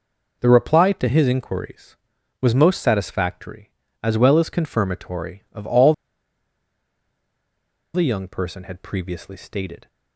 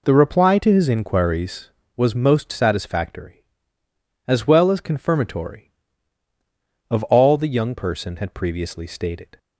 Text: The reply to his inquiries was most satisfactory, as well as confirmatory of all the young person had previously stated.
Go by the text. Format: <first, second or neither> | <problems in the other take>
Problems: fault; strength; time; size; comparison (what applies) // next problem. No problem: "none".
second | pauses between "all" and "the"; strong; at 5.9 s; 2.0 s long